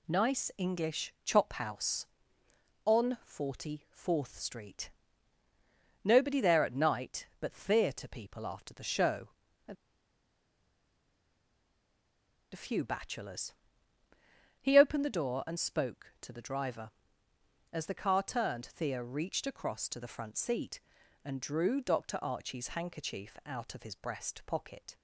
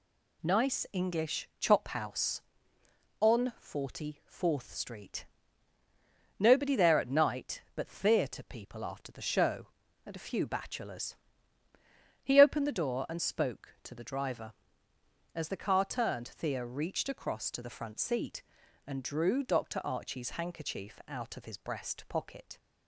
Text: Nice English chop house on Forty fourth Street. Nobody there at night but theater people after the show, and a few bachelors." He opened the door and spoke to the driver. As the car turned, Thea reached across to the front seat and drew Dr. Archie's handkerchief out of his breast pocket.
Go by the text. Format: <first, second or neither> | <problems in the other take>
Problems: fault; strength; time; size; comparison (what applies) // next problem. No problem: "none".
second | pauses between "and" and "a"; strong; at 9.7 s; 2.7 s long